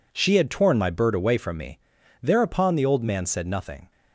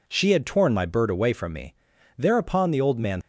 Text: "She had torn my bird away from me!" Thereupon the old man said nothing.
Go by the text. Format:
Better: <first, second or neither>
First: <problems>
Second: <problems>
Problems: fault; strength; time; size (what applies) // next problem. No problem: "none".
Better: first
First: none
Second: stops before "said nothing"; at 3.2 s